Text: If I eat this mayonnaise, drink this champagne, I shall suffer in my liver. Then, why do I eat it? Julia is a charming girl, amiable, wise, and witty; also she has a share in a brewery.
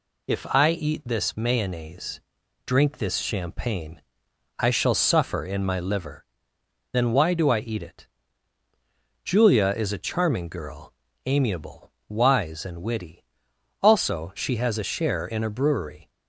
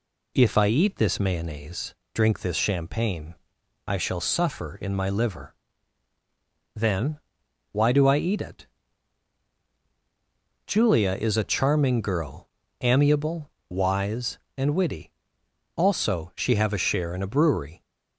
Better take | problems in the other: first | says "have" for "has"; at 16.5 s

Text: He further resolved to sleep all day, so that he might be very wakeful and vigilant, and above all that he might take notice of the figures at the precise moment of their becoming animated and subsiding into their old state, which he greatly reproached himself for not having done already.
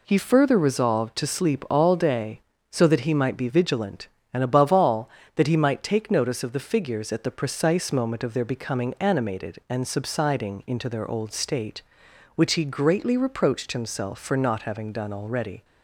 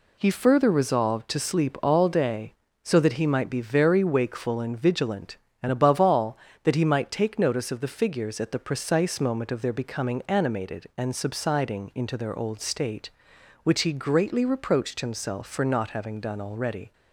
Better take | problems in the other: second | skips "very wakeful and"; at 3.4 s

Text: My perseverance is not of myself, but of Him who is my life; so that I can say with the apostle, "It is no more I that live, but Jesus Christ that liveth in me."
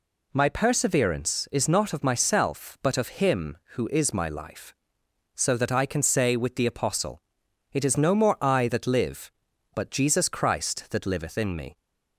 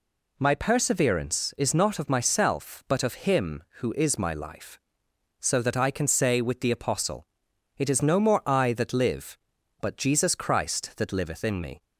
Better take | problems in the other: neither | none

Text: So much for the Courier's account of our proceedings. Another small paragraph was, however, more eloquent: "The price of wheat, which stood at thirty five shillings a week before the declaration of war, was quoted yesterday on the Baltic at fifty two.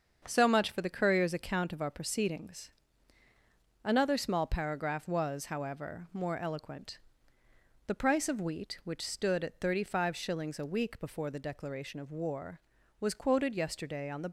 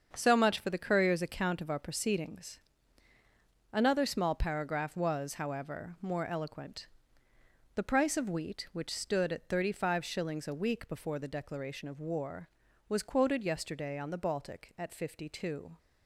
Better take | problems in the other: second | starts louder than the rest; until 1.2 s; 7 dB; also in the second // stops before "Baltic at fifty two"; at 14.2 s

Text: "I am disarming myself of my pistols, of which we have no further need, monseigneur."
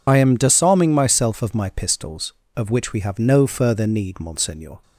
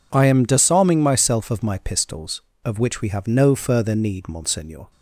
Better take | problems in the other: second | loses the start of "I"; at 0.0 s; 40 ms

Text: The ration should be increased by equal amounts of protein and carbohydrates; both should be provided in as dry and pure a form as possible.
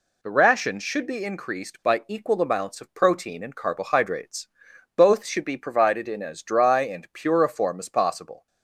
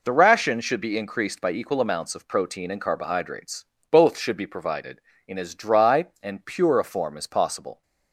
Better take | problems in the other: neither | none

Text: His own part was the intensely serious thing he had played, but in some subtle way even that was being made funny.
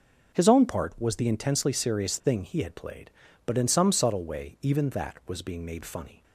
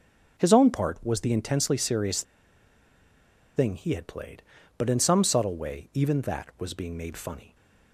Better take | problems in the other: first | pauses between "serious" and "thing"; strong; at 2.2 s; 1.3 s long

